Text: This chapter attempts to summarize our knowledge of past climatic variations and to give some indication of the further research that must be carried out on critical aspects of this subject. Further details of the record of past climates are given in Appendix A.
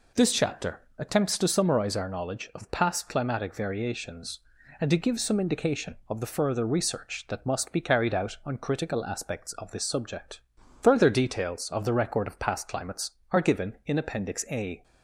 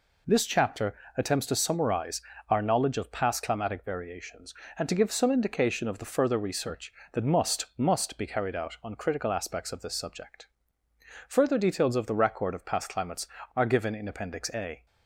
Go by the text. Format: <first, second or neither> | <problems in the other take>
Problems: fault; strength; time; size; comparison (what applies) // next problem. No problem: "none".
first | pauses between "chapter" and "attempts"; slight; at 0.9 s; 0.22 s long; slight in the first // pauses between "summarize" and "our"; slight; at 2.1 s; 0.30 s long // says "must" twice; at 7.7 s